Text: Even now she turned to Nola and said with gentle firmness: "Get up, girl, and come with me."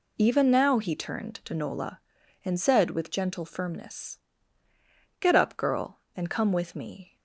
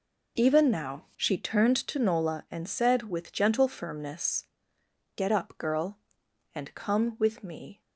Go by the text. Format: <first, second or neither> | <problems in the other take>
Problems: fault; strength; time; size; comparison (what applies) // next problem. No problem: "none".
second | says "he" for "she"; at 0.7 s